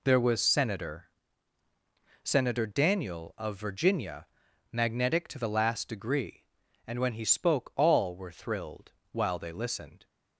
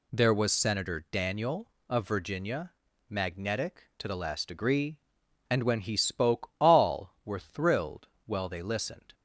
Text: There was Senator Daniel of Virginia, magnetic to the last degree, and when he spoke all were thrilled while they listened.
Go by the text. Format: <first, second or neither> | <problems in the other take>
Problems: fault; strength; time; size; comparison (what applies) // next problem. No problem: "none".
second | says "Senator" twice; at 2.2 s // pauses between "thrilled" and "while"; slight; at 8.9 s; 0.18 s long; slight in the second